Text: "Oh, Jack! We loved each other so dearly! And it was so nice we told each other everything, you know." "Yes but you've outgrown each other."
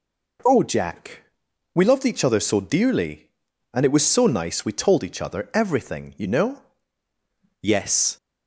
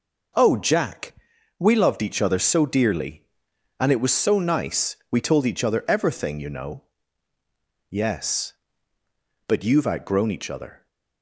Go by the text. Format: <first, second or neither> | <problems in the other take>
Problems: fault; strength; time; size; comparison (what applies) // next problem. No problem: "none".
second | stops before "but you've outgrown each other"; at 8.1 s